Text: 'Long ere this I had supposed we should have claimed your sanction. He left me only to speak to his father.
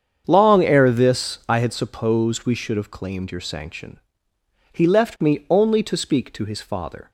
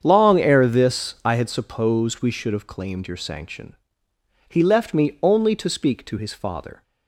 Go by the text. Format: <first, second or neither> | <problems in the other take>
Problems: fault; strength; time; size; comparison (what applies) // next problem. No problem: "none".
neither | starts louder than the rest; strong; the same in both